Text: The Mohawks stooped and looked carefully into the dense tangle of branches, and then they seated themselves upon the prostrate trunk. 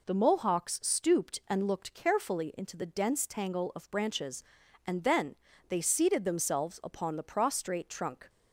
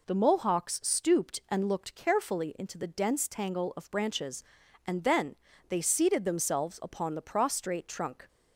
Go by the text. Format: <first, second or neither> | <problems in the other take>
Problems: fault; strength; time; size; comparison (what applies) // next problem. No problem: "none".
neither | pauses between "then" and "they"; slight; the same in both